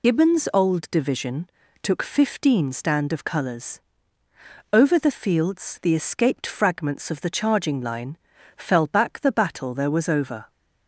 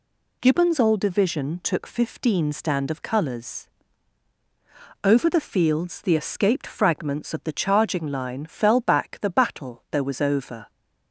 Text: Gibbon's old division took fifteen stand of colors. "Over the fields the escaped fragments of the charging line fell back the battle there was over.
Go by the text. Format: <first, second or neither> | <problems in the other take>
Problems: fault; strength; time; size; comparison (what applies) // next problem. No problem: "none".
second | loses the start of "Gibbon's"; at 0.0 s; 45 ms // pauses between "division" and "took"; slight; at 1.4 s; 0.32 s long // pauses between "line" and "fell"; at 8.1 s; 0.40 s long